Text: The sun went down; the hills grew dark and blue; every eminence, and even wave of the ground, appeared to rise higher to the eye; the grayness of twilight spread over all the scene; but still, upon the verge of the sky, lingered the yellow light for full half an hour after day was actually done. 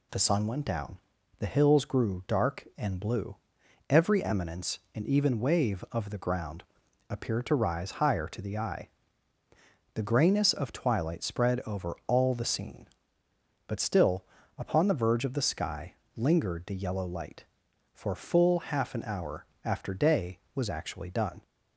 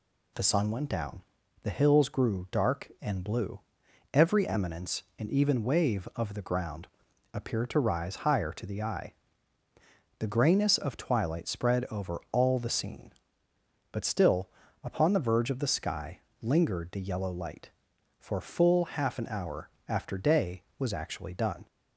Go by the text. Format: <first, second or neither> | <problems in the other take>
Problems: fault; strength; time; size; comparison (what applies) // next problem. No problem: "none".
neither | pauses between "hour" and "after"; slight; the same in both